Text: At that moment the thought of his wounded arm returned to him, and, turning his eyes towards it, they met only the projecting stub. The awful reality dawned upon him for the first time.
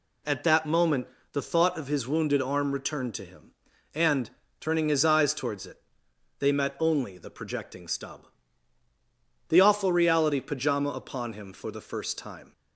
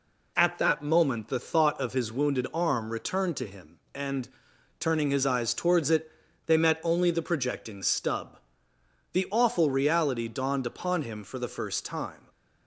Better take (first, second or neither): second